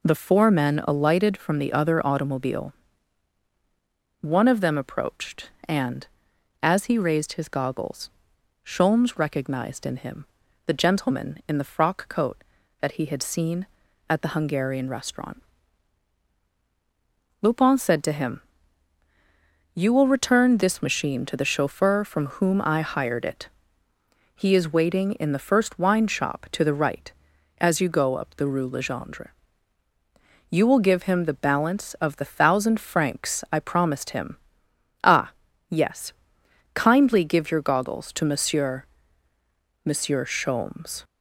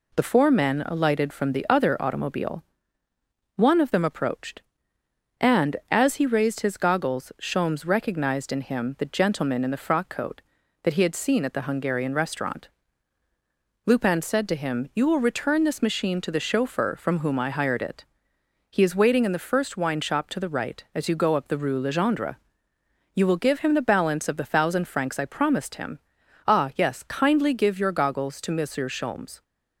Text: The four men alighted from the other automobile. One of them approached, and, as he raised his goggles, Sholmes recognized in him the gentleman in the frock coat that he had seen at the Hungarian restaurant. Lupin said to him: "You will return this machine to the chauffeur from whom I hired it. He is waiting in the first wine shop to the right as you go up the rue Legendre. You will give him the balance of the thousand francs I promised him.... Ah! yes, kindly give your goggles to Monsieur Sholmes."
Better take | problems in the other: second | pauses between "him" and "the"; at 10.2 s; 0.40 s long // says "Monsieur" twice; at 39.8 s

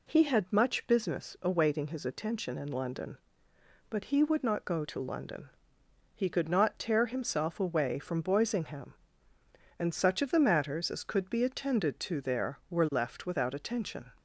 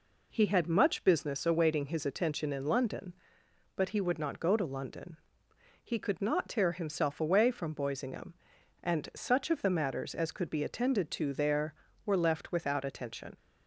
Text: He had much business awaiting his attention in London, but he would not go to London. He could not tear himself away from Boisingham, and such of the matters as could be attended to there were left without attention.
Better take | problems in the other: neither | none

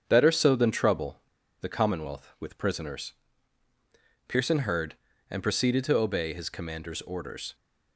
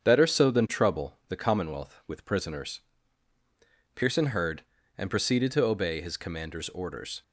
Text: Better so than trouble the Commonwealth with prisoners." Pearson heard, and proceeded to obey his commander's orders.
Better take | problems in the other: second | starts louder than the rest; strong; until 1.0 s; 7.5 dB; strong in the second // pauses between "trouble" and "the"; at 1.1 s; 0.41 s long

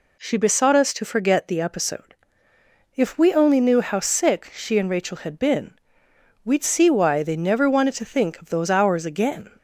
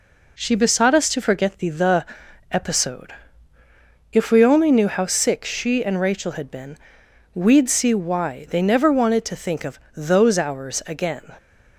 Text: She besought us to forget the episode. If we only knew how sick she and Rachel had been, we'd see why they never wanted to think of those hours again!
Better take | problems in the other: first | says "the" twice; at 1.6 s // pauses between "of" and "those"; slight; at 9.7 s; 0.16 s long

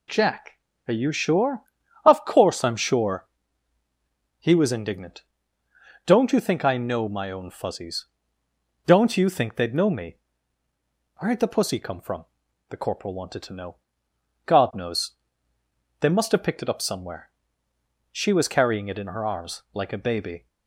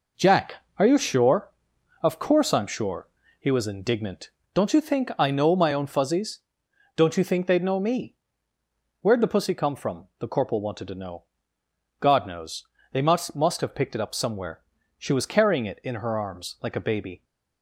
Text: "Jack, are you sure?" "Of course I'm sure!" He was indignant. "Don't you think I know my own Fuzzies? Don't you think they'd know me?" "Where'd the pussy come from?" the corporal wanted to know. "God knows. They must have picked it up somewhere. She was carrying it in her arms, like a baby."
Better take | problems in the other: first | says "must" twice; at 13.3 s

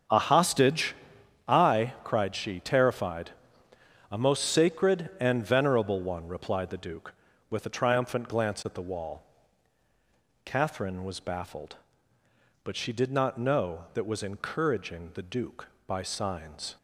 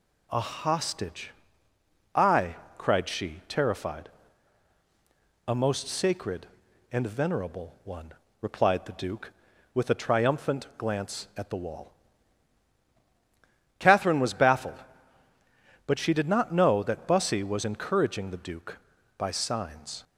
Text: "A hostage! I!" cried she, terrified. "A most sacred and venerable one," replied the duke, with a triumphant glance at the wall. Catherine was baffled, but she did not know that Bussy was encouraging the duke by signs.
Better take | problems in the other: second | starts louder than the rest; strong; until 1.6 s; 7.5 dB // skips "Bussy"; at 14.0 s

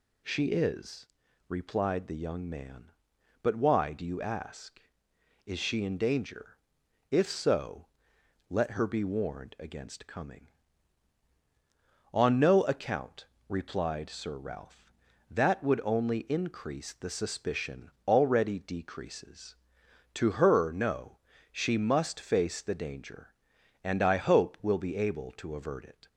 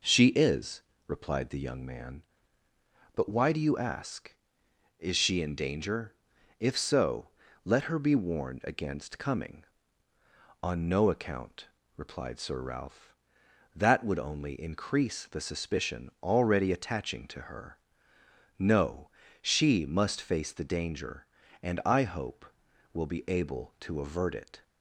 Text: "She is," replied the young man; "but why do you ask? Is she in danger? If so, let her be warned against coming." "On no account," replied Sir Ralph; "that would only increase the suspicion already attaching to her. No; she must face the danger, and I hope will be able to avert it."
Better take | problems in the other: second | pauses between "suspicion" and "already"; slight; at 17.8 s; 0.18 s long // says "decreases" for "attaching"; at 18.5 s

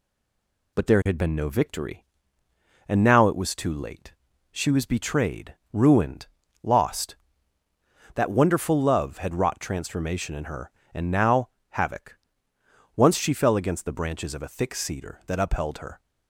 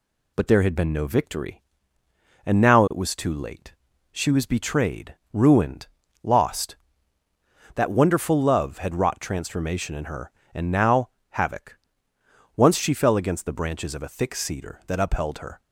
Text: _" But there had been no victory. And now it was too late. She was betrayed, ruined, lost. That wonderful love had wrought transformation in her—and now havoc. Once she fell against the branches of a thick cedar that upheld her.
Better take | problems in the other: second | stays silent before the first word; slight; until 0.7 s; 0.7 s long // pauses between "now" and "havoc"; slight; at 11.4 s; 0.20 s long; slight in the second

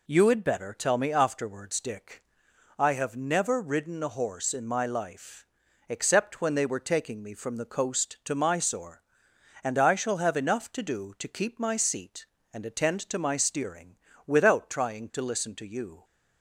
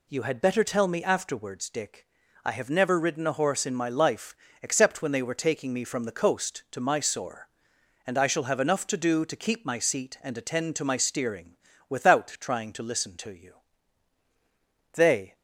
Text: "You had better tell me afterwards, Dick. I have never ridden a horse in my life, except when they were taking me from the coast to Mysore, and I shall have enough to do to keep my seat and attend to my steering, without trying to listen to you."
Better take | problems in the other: first | goes on to say "They"; slight; from 14.9 s on; 0.42 s long

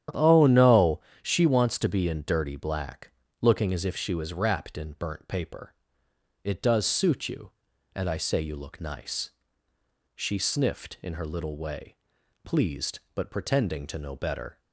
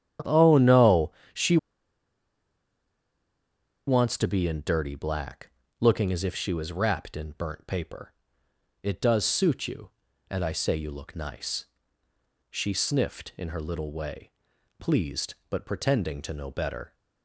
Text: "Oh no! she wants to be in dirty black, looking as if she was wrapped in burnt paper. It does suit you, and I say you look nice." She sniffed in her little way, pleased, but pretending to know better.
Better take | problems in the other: first | starts louder than the rest; strong; until 1.4 s; 10 dB; strong in the first // pauses between "she" and "wants"; strong; at 1.5 s; 2.3 s long

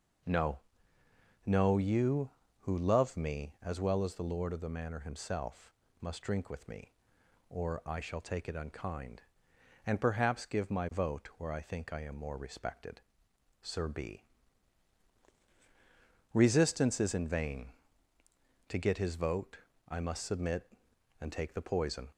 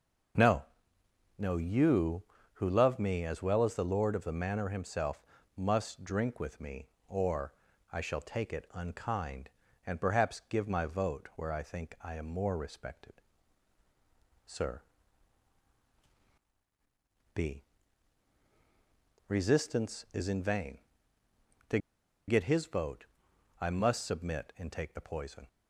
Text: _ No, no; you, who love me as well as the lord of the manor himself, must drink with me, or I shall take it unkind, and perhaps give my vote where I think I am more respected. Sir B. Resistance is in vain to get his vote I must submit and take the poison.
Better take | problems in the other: first | pauses between "or" and "I"; slight; at 7.5 s; 0.36 s long // pauses between "Sir" and "B"; strong; at 14.8 s; 2.5 s long // pauses between "to" and "get"; noticeable; at 21.7 s; 0.49 s long // pauses between "vote" and "I"; noticeable; at 23.0 s; 0.54 s long; slight in the first

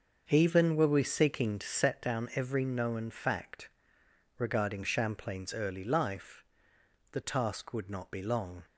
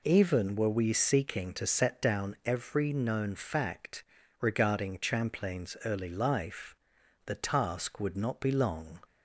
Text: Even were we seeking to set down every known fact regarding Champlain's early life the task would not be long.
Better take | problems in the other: second | starts louder than the rest; until 1.9 s; 6.5 dB // pauses between "fact" and "regarding"; noticeable; at 3.6 s; 0.72 s long; also in the second // pauses between "life" and "the"; noticeable; at 6.4 s; 0.70 s long; noticeable in the second

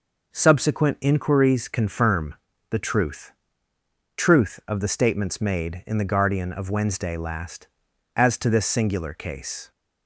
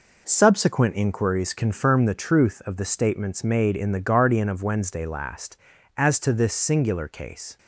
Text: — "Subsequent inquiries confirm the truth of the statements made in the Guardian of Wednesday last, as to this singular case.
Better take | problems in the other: second | pauses between "confirm" and "the"; slight; at 2.3 s; 0.34 s long // says "truth" twice; at 4.1 s

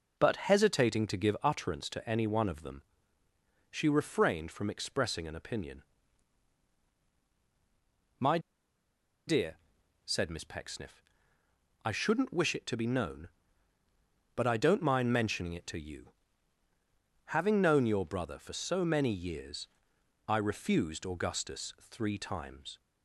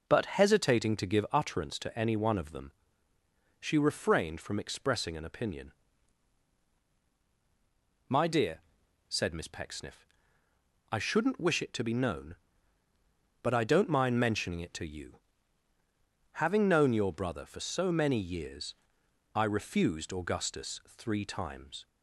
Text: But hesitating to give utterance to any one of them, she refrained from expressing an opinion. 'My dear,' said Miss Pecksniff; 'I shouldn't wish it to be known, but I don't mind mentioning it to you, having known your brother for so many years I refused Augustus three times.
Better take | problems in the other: second | pauses between "My" and "dear"; noticeable; at 8.3 s; 0.88 s long // pauses between "years" and "I"; noticeable; at 19.6 s; 0.62 s long; noticeable in the second

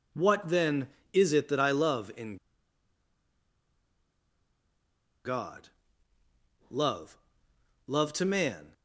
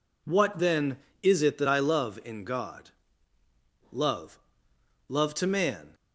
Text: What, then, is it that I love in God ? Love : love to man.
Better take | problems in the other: second | pauses between "in" and "God"; strong; at 2.3 s; 2.8 s long

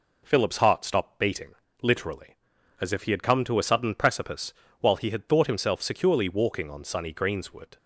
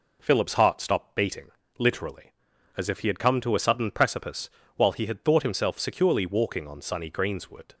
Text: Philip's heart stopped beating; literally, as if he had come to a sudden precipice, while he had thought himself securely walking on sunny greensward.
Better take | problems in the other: neither | none

